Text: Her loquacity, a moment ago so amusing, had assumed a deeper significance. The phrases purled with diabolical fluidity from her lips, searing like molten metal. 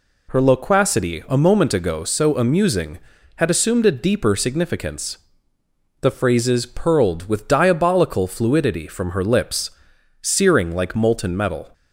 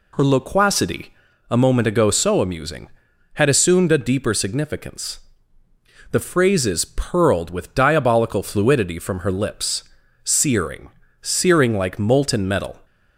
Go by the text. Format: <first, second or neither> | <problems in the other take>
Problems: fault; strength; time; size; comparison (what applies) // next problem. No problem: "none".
first | says "searing" twice; at 11.2 s